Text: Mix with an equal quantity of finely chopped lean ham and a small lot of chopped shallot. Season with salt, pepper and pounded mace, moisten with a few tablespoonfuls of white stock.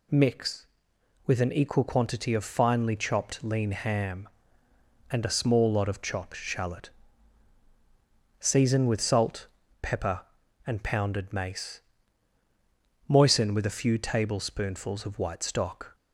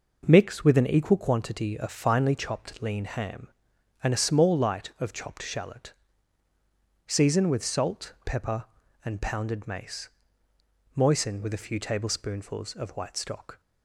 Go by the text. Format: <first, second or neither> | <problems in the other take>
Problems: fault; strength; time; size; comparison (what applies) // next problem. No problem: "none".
first | says "light" for "lot"; at 4.5 s